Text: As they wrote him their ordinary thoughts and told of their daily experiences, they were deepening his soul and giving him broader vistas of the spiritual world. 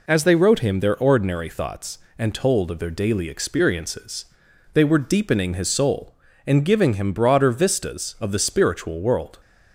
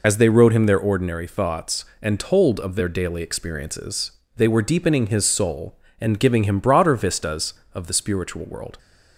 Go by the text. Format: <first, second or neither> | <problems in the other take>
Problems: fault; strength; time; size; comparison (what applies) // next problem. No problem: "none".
first | loses the start of "As"; at 0.0 s; 50 ms